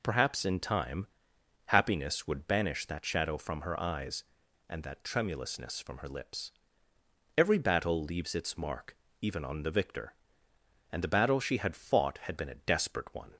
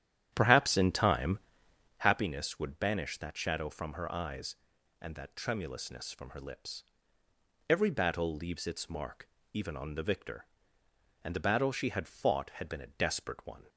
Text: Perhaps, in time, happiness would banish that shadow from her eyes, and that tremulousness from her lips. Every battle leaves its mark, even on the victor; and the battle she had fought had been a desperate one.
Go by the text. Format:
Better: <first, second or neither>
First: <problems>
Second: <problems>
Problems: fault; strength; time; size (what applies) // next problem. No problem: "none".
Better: first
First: none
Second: starts louder than the rest; strong; until 2.1 s; 10.5 dB